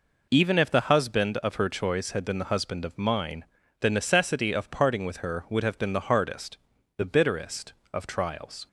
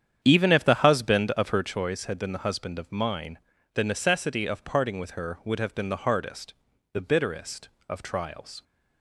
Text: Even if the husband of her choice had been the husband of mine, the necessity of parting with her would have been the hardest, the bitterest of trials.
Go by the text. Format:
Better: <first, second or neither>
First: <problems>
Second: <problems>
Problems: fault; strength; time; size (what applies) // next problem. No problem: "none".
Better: first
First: none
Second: starts louder than the rest; strong; until 1.7 s; 9 dB